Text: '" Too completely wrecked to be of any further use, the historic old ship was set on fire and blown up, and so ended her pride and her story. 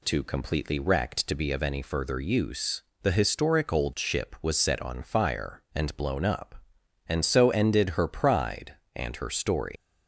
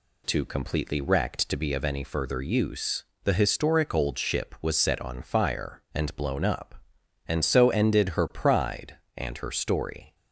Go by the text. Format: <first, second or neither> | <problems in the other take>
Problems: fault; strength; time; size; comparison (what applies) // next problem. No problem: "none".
second | leaves "story" unfinished; at 9.7 s; 175 ms